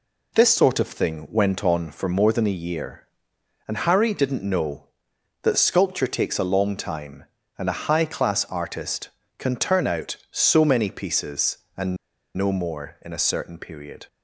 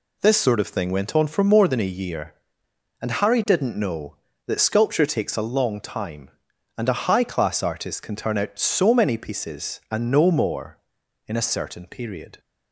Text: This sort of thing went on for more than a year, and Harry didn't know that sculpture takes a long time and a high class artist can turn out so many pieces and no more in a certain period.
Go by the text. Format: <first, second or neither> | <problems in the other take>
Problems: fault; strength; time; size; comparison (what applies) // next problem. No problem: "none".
second | pauses between "and" and "no"; at 11.9 s; 0.40 s long